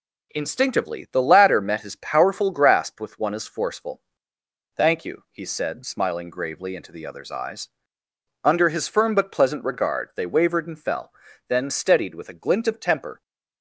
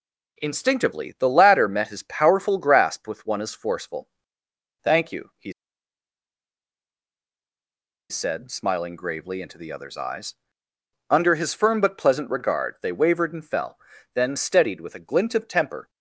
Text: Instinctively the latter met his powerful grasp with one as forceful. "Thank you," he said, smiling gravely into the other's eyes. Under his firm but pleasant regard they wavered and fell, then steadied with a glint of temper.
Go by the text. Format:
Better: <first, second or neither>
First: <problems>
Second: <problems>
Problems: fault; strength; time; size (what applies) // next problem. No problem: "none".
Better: first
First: none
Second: pauses between "he" and "said"; strong; at 5.5 s; 2.5 s long